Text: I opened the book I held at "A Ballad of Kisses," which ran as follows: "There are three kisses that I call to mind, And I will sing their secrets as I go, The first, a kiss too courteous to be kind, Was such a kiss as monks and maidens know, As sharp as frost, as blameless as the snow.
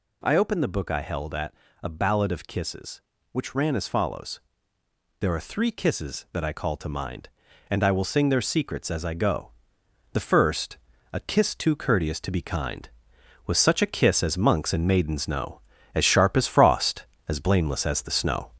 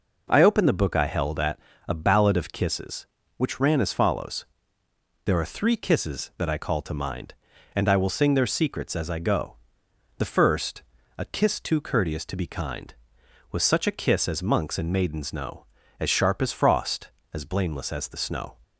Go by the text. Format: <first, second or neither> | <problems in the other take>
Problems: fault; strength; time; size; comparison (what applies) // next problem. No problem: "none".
second | gets louder; noticeable; throughout; 4 dB // pauses between "at" and "A"; slight; at 1.5 s; 0.30 s long; slight in the second